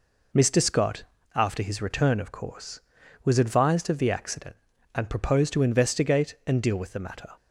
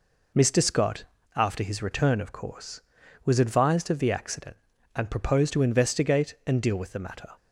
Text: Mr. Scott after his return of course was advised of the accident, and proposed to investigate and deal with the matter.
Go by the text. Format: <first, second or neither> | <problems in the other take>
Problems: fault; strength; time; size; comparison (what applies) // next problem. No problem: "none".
neither | pauses between "Scott" and "after"; slight; the same in both